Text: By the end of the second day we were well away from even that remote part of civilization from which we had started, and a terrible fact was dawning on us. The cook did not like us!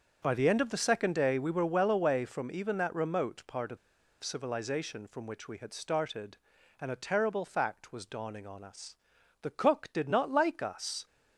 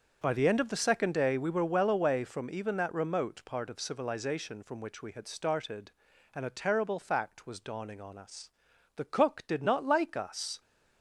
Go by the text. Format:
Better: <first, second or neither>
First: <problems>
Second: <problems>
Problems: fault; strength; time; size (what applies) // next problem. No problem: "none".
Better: second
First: starts louder than the rest; until 1.2 s; 7 dB // pauses between "of" and "civilization"; at 3.7 s; 0.45 s long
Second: starts louder than the rest; until 1.2 s; 7 dB